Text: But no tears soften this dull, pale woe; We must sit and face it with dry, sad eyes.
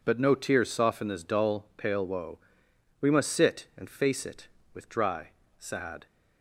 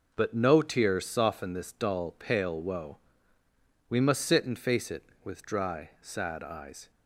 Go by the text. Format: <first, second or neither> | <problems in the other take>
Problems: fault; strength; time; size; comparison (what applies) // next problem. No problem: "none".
second | stops before "eyes"; at 6.0 s